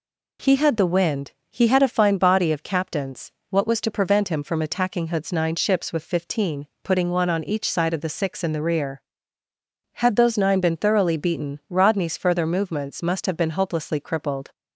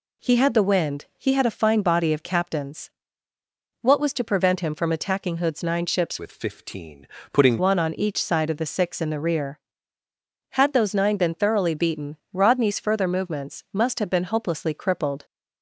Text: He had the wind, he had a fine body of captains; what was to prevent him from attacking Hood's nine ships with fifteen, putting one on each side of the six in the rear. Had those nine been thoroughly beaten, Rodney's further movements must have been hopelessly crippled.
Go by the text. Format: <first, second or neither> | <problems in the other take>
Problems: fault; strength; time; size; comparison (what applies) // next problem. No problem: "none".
first | changes voice from "with" to "putting"; from 6.1 to 7.6 s; 1.5 s long